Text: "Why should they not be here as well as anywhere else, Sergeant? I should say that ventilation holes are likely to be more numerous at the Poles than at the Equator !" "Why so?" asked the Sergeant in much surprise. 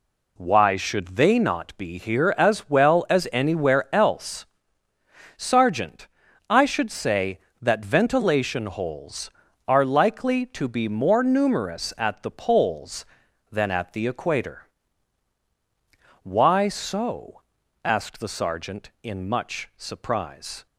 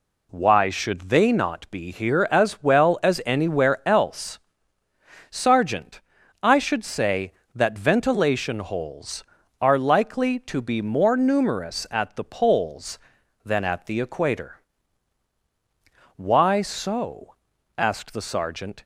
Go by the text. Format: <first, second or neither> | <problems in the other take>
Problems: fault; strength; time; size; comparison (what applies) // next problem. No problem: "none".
first | stops before "in much surprise"; at 18.8 s